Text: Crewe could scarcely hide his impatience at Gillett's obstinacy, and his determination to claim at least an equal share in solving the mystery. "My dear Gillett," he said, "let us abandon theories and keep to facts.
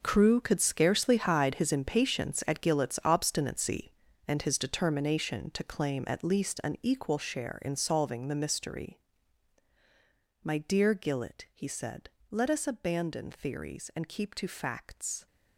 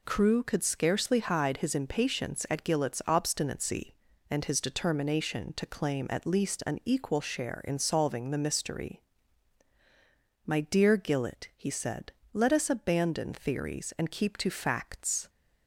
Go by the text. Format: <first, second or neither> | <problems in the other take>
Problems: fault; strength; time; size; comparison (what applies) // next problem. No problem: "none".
second | gets quieter; strong; throughout; 13.5 dB